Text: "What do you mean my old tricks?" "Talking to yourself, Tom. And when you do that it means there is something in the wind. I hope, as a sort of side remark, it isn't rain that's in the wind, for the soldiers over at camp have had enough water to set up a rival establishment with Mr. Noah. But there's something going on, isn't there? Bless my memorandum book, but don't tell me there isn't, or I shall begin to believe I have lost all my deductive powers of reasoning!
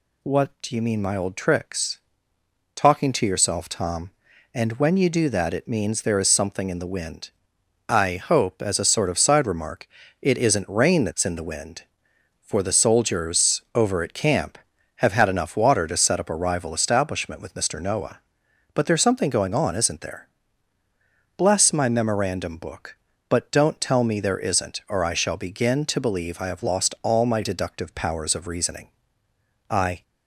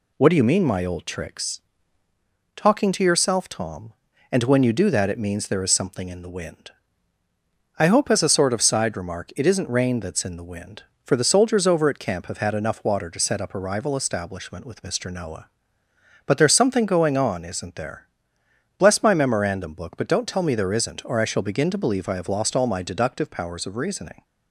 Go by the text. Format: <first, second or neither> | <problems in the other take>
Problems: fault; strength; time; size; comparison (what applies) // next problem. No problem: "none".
second | goes on to say "I"; slight; from 29.6 s on; 0.34 s long